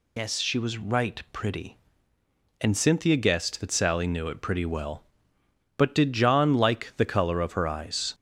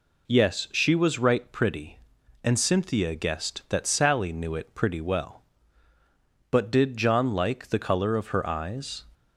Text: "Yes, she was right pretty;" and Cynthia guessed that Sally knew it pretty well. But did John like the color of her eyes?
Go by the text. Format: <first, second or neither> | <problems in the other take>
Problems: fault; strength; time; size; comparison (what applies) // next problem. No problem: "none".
second | loses the start of "Yes"; at 0.1 s; 80 ms